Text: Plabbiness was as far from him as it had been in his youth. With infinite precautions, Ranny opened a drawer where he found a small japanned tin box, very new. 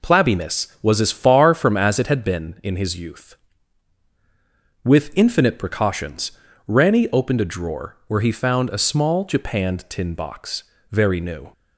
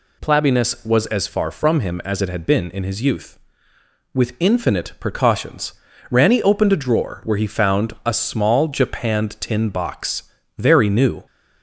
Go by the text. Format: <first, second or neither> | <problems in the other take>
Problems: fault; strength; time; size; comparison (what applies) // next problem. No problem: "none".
second | skips "him"; at 1.7 s